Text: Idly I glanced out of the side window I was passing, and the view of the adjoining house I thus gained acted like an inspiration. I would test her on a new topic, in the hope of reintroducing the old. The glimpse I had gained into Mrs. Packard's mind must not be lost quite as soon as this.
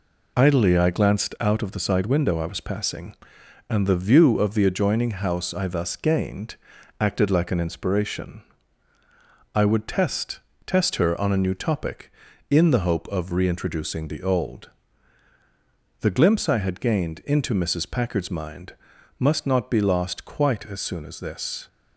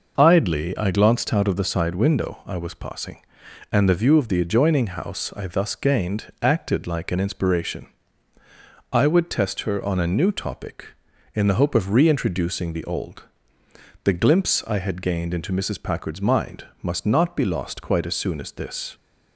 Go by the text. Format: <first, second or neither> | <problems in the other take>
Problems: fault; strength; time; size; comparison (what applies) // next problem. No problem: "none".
second | pauses between "gained" and "acted"; at 6.5 s; 0.44 s long // says "test" twice; at 10.6 s // pauses between "mind" and "must"; noticeable; at 18.7 s; 0.46 s long; slight in the second